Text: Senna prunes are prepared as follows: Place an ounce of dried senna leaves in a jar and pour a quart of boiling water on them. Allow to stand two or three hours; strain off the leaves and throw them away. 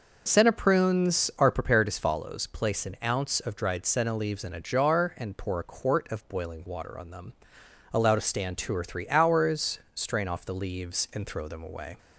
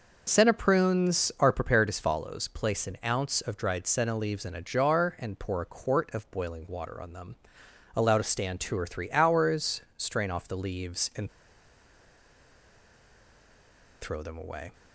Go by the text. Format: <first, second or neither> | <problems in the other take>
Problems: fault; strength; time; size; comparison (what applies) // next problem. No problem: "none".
first | pauses between "and" and "throw"; strong; at 11.2 s; 2.7 s long